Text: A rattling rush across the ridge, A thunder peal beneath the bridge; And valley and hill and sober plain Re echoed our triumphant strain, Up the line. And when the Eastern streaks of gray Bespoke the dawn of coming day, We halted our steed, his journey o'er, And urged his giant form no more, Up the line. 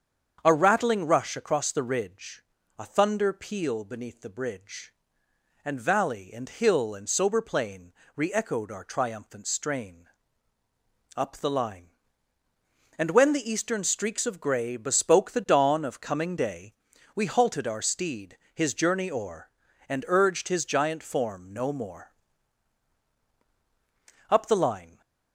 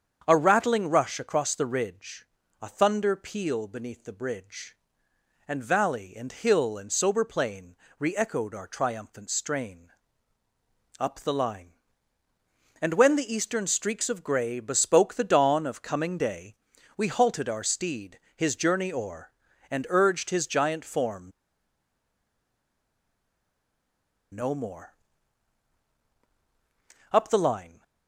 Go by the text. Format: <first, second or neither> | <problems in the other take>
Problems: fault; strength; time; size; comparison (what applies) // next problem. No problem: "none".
first | starts louder than the rest; strong; until 1.2 s; 7.5 dB; strong in the first // pauses between "plain" and "Re"; slight; at 7.7 s; 0.24 s long; slight in the first // pauses between "form" and "no"; strong; at 21.3 s; 3.0 s long